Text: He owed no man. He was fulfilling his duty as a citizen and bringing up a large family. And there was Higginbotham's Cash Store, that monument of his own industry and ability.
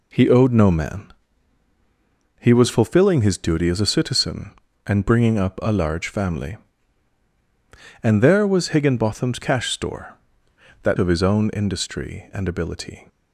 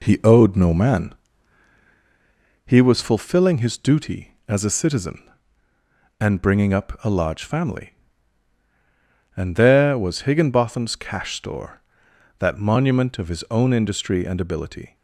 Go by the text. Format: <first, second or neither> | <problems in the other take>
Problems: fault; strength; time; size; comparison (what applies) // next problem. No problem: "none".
second | skips "monument"; at 10.9 s